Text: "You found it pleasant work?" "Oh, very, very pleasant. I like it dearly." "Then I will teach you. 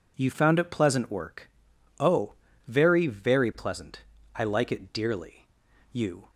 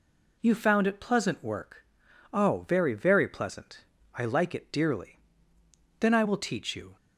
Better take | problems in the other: second | skips "Then I will teach"; at 5.7 s

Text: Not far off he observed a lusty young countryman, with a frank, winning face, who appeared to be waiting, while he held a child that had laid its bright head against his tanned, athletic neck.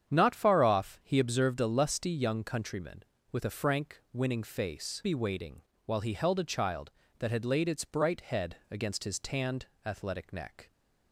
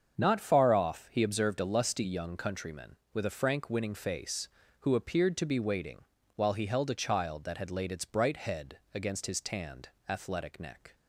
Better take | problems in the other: second | starts louder than the rest; strong; until 1.1 s; 8.5 dB; strong in the second // skips "who appeared to"; at 5.0 s // pauses between "head" and "against"; slight; at 8.5 s; 0.16 s long; slight in the second

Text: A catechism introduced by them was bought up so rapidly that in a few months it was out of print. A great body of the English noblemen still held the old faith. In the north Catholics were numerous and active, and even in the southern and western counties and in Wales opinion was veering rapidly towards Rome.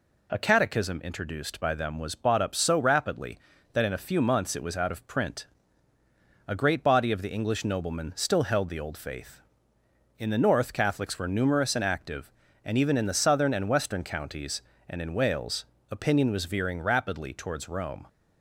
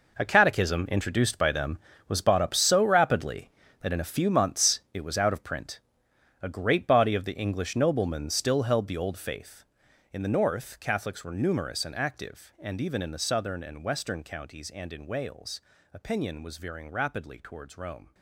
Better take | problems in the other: first | gets quieter; strong; throughout; 13.5 dB // pauses between "Wales" and "opinion"; slight; at 15.5 s; 0.32 s long; slight in the first

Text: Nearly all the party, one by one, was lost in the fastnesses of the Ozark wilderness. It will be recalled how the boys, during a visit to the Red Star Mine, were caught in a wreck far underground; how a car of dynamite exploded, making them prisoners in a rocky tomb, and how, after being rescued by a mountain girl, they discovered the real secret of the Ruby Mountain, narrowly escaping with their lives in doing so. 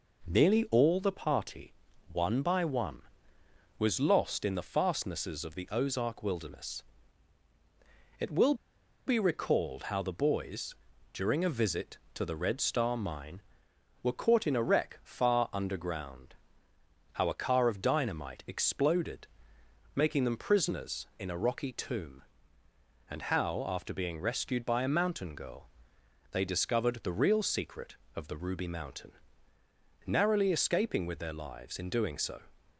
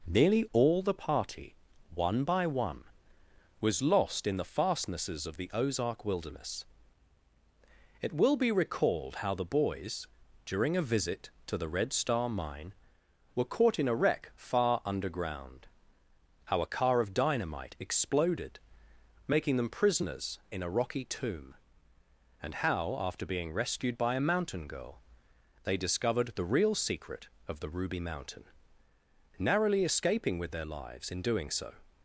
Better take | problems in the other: second | pauses between "will" and "be"; noticeable; at 8.5 s; 0.52 s long

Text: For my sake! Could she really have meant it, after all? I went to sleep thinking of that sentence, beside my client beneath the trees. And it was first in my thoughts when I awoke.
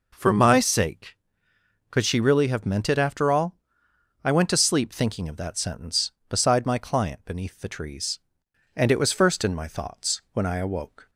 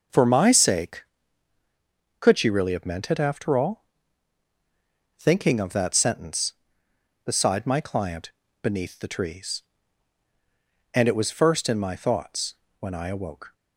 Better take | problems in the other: first | skips "I went to sleep"; at 4.5 s // pauses between "client" and "beneath"; slight; at 8.3 s; 0.32 s long // pauses between "thoughts" and "when"; slight; at 12.5 s; 0.24 s long

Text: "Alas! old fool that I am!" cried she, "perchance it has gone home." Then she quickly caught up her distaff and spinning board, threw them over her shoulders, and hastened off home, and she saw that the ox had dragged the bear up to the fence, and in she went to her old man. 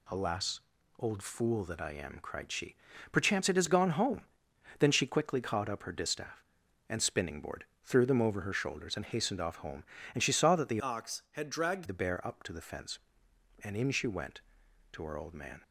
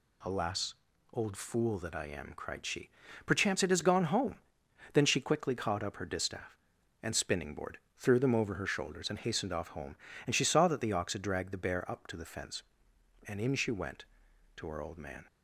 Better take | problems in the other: second | changes voice from "ox" to "dragged"; from 10.8 to 11.8 s; 1.0 s long

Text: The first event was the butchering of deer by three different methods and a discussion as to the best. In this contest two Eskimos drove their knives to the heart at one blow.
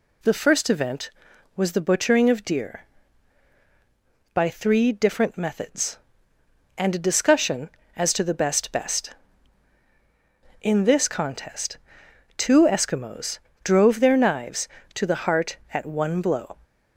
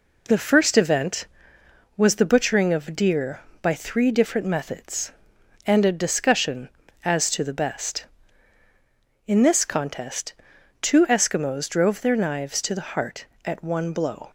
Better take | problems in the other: second | says "best" twice; at 8.7 s // pauses between "contest" and "two"; noticeable; at 11.7 s; 0.58 s long; noticeable in the second // pauses between "Eskimos" and "drove"; slight; at 13.3 s; 0.24 s long

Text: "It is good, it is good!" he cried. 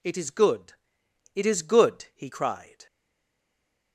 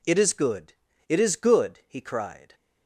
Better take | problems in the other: second | stays silent after the last word; from 2.8 s on; 1.1 s long

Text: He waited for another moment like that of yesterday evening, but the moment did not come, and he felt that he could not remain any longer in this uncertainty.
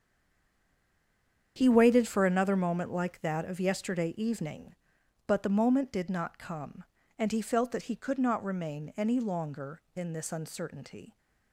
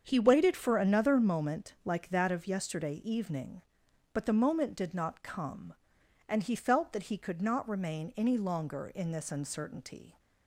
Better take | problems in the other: second | stays silent before the first word; noticeable; until 1.5 s; 1.5 s long // starts louder than the rest; strong; until 2.5 s; 8 dB; strong in the second

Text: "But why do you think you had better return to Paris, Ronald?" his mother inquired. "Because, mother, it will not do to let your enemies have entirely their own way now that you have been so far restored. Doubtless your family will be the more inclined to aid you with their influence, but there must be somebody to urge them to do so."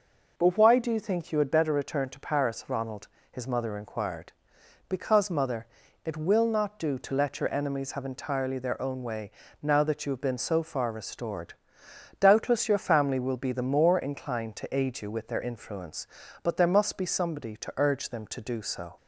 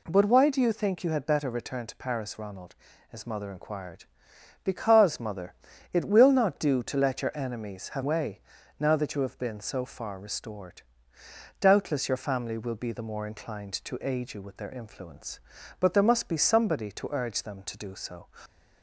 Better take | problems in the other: first | skips "entirely their own"; at 8.0 s // pauses between "way" and "now"; at 8.3 s; 0.40 s long; slight in the first

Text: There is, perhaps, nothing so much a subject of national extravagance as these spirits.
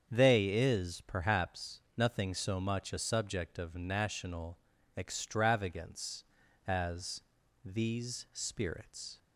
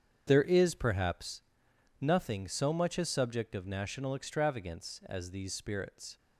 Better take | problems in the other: second | starts louder than the rest; strong; until 1.1 s; 7 dB; strong in the second // says "They" for "There"; at 0.0 s // pauses between "national" and "extravagance"; at 4.5 s; 0.40 s long // pauses between "as" and "these"; at 7.2 s; 0.42 s long

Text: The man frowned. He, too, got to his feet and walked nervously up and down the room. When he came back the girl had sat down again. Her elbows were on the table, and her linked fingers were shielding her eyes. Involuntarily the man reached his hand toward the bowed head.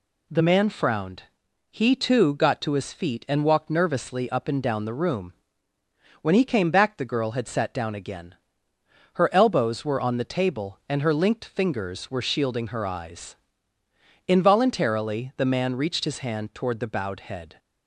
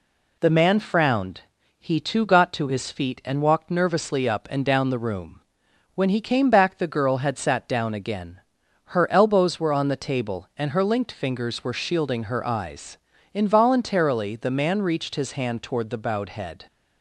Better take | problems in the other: neither | none

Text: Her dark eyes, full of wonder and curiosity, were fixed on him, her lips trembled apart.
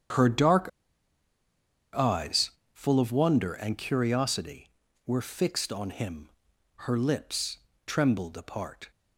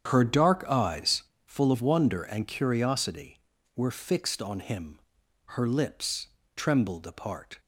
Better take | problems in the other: second | starts louder than the rest; strong; until 2.4 s; 8.5 dB; strong in the second // pauses between "dark" and "eyes"; strong; at 0.6 s; 1.2 s long // pauses between "lips" and "trembled"; slight; at 7.5 s; 0.30 s long; slight in the second

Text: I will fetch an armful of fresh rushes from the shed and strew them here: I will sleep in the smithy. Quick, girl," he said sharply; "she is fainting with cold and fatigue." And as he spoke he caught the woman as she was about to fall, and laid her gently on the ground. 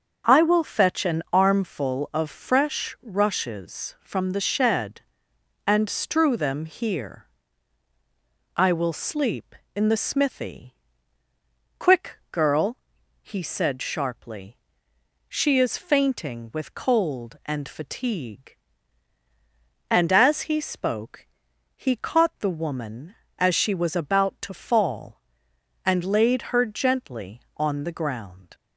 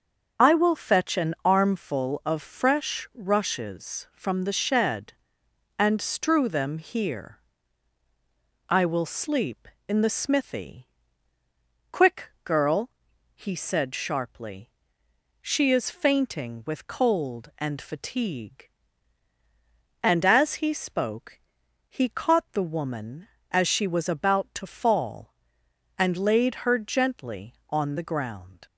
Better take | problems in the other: first | loses the start of "I"; at 0.3 s; 35 ms // starts louder than the rest; until 1.5 s; 7 dB; also in the first // pauses between "spoke" and "he"; noticeable; at 21.3 s; 0.50 s long; noticeable in the first

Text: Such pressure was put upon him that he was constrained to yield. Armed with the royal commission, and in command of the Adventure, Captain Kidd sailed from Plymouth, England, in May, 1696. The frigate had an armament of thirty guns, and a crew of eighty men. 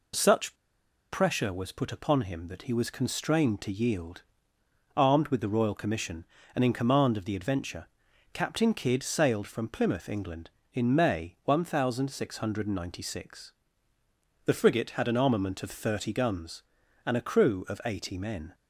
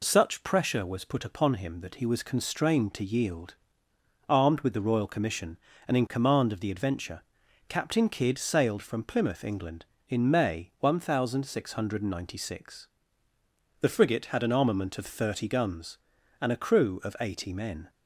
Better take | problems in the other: second | pauses between "Such" and "pressure"; noticeable; at 0.5 s; 0.57 s long

